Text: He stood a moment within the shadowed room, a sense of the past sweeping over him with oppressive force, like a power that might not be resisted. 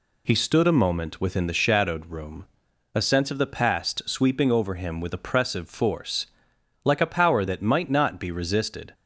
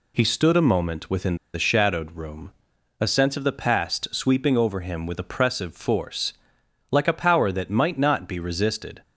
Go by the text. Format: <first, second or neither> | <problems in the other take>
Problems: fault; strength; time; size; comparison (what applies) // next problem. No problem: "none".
first | pauses between "within" and "the"; slight; at 1.3 s; 0.18 s long